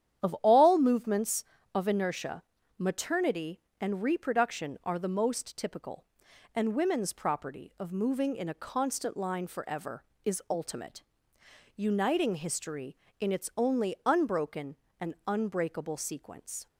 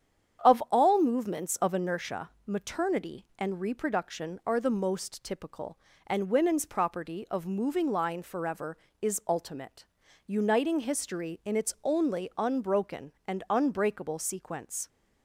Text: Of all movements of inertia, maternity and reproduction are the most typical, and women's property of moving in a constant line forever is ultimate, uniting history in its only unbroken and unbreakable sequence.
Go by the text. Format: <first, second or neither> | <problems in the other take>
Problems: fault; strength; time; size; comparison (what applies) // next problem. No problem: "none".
first | starts louder than the rest; strong; until 1.5 s; 8.5 dB; strong in the first // skips "in a constant"; at 7.9 s